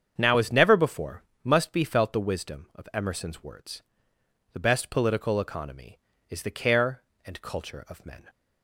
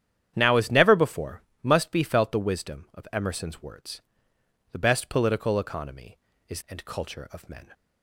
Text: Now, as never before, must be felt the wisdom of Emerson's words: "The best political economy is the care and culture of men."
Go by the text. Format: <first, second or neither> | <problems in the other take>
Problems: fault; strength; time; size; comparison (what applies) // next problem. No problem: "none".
first | starts louder than the rest; strong; until 1.3 s; 9.5 dB; strong in the first // skips "the care"; at 6.6 s